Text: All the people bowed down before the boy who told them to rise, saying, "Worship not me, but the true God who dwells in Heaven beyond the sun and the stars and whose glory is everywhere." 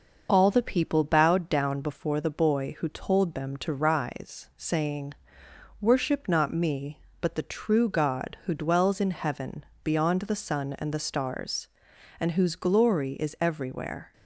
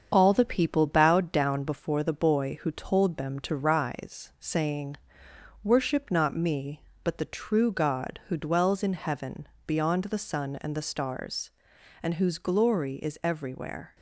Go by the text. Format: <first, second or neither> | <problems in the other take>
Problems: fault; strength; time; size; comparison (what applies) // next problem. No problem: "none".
first | gets quieter; slight; throughout; 3.5 dB // pauses between "Heaven" and "beyond"; slight; at 9.4 s; 0.18 s long; slight in the first